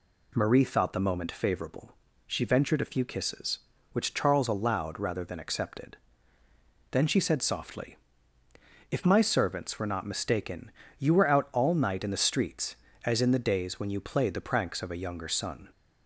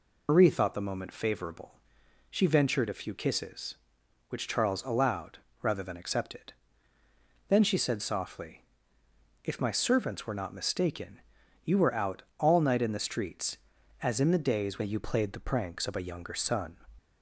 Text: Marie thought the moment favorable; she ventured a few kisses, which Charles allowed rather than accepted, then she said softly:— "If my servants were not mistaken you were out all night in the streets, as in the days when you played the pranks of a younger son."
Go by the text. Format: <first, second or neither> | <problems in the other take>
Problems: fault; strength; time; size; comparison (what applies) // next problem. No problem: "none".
first | loses the start of "Marie"; at 0.2 s; 75 ms // pauses between "allowed" and "rather"; slight; at 5.3 s; 0.22 s long // pauses between "mistaken" and "you"; noticeable; at 11.1 s; 0.46 s long; slight in the first // pauses between "out" and "all"; slight; at 12.2 s; 0.16 s long